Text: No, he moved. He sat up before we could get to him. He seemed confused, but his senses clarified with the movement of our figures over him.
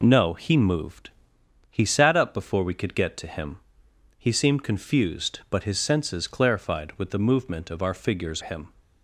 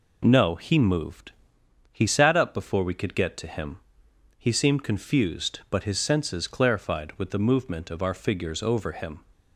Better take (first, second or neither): second